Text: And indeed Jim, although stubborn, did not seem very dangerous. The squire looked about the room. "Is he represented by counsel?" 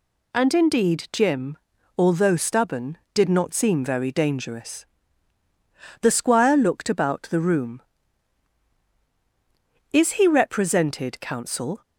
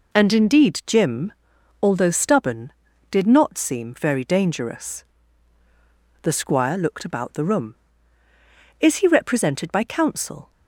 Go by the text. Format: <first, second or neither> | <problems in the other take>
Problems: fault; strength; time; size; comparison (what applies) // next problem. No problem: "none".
second | skips "by"; at 11.1 s